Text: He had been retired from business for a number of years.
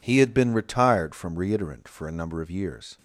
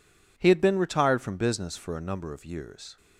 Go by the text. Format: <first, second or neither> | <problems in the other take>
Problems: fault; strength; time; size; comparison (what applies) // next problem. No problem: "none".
second | says "reiterant" for "business"; at 1.3 s